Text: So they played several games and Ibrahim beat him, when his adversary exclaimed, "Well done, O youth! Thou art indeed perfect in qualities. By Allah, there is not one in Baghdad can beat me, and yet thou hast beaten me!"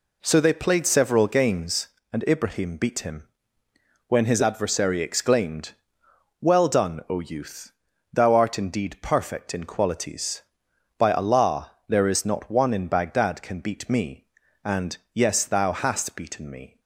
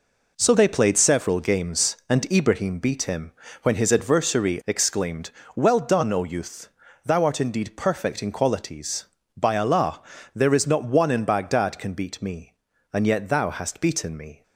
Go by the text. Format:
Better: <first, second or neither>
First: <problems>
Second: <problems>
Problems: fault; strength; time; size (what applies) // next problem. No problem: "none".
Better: second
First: says "yes" for "yet"; at 15.1 s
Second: none